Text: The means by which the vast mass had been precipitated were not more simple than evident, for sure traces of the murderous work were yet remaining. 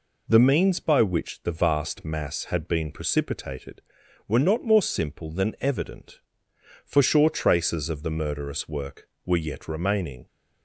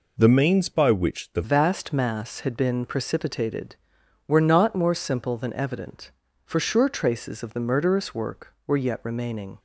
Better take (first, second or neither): first